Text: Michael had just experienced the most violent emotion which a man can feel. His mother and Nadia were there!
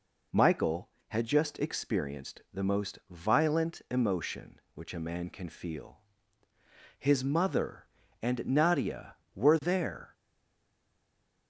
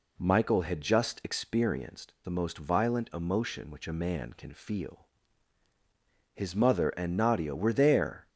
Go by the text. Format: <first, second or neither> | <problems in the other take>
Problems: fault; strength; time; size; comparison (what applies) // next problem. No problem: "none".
second | stays silent after the last word; noticeable; from 10.1 s on; 1.3 s long